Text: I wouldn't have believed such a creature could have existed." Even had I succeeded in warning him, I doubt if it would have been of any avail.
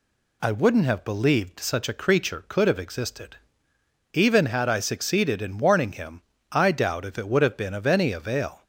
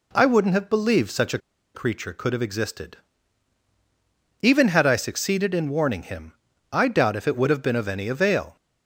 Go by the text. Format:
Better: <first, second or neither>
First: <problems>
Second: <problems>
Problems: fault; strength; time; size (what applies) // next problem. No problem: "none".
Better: first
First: none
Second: pauses between "a" and "creature"; at 1.3 s; 0.36 s long